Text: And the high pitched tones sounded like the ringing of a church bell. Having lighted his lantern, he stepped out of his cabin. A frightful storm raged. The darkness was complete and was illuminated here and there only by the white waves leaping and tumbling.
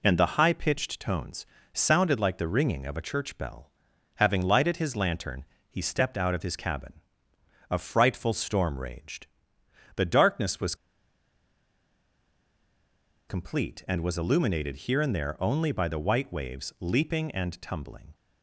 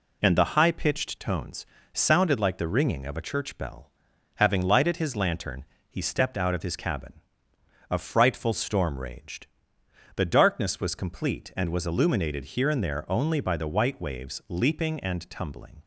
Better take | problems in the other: second | pauses between "tones" and "sounded"; slight; at 1.4 s; 0.26 s long; slight in the second // pauses between "was" and "complete"; strong; at 10.7 s; 2.5 s long

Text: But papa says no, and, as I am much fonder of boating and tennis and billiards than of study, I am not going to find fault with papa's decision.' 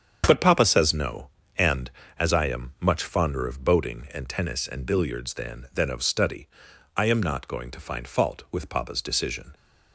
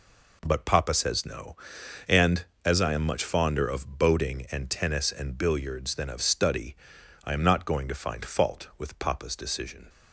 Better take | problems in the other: second | starts louder than the rest; strong; until 1.2 s; 7.5 dB // says "than" twice; at 5.7 s

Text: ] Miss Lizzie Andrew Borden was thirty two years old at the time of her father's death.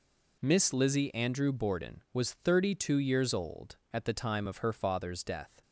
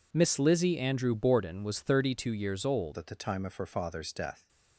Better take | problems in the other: first | changes voice at "at"; from 2.9 s on; 1.5 s long

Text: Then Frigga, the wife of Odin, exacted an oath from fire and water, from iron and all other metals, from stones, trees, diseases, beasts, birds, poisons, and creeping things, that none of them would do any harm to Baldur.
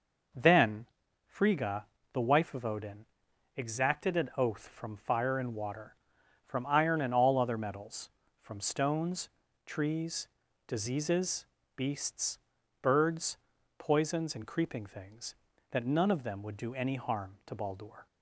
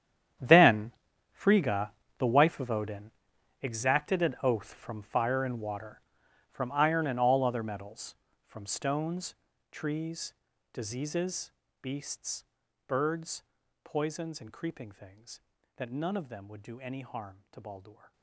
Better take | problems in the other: first | gets quieter; strong; throughout; 15.5 dB // pauses between "Then" and "Frigga"; at 0.9 s; 0.40 s long; also in the first

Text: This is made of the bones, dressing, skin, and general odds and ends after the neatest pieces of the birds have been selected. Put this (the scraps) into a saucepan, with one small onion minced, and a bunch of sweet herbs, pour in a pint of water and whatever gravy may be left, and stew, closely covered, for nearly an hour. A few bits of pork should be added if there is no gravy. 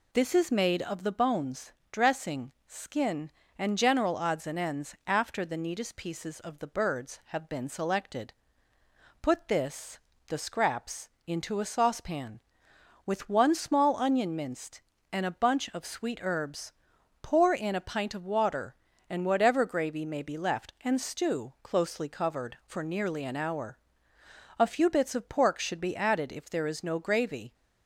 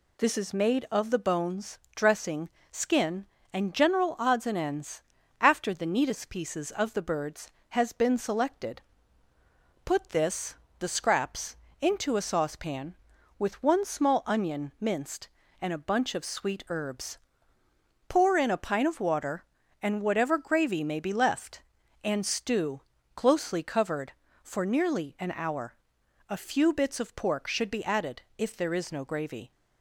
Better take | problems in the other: first | pauses between "ends" and "after"; at 5.0 s; 0.40 s long // says "has" for "have"; at 7.6 s // pauses between "added" and "if"; slight; at 28.2 s; 0.16 s long

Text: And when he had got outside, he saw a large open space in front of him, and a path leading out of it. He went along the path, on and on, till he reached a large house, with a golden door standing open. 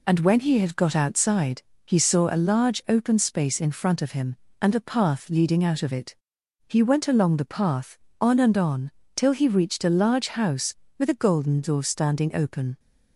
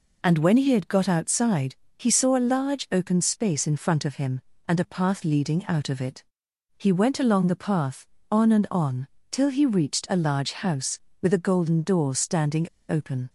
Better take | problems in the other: first | pauses between "standing" and "open"; slight; at 12.6 s; 0.21 s long

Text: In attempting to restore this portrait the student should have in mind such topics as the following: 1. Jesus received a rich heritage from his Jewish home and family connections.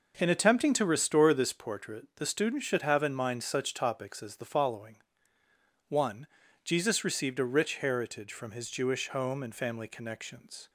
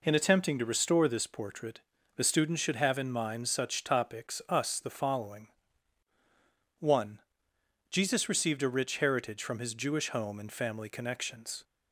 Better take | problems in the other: first | pauses between "portrait" and "the"; at 1.7 s; 0.38 s long // says "us" for "as"; at 4.4 s

